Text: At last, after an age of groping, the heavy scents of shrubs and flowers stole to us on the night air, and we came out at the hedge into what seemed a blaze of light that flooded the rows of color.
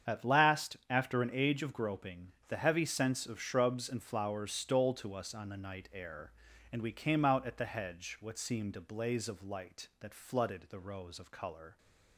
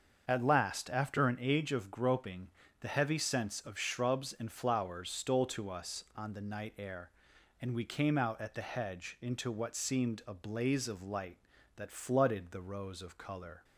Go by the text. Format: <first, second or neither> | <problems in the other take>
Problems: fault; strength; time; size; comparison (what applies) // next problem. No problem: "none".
second | starts louder than the rest; strong; until 1.1 s; 7.5 dB; also in the second // skips "into"; at 8.1 s